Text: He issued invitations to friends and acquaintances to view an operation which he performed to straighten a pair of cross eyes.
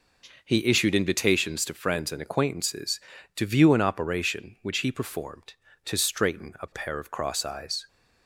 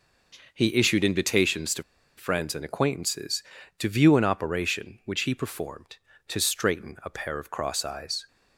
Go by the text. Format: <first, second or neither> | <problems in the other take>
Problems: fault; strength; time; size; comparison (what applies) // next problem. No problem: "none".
first | pauses between "to" and "friends"; slight; at 1.8 s; 0.33 s long